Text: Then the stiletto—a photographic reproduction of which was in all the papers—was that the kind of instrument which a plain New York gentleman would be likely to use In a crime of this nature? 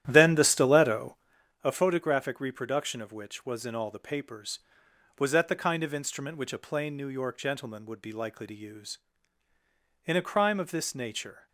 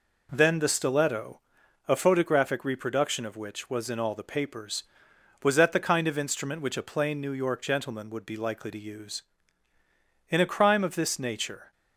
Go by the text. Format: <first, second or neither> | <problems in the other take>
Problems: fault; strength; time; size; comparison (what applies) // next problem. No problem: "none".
second | starts louder than the rest; strong; until 1.4 s; 11.5 dB